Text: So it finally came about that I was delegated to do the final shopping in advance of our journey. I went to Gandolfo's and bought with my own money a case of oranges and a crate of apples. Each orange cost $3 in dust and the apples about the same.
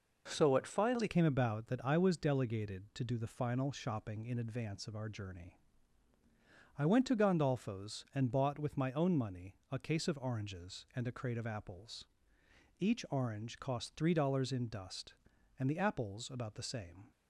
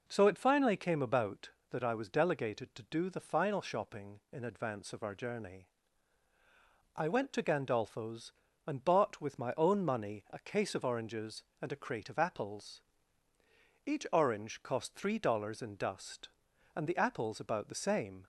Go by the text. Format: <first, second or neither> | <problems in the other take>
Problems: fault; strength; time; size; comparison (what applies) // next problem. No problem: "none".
second | changes voice at "came"; from 1.0 s on; 16.1 s long // pauses between "money" and "a"; slight; at 9.5 s; 0.16 s long